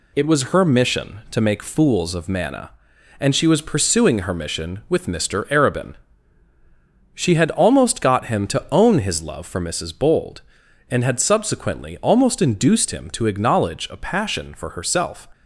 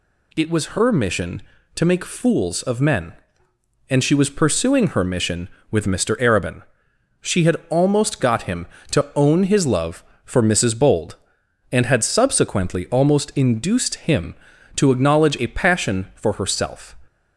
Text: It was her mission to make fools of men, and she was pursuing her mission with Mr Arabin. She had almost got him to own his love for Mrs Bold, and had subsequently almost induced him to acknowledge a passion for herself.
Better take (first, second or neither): second